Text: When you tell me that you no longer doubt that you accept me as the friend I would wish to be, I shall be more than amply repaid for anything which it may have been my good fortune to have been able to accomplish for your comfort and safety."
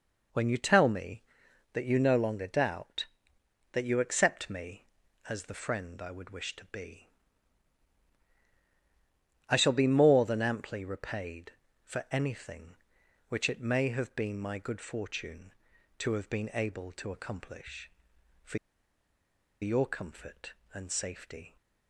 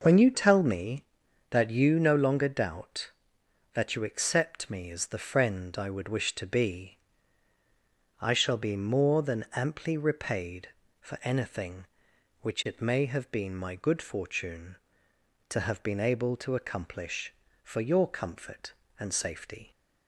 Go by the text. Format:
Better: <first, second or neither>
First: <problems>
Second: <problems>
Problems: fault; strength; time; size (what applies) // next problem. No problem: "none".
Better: second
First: pauses between "for" and "your"; at 18.5 s; 1.0 s long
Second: none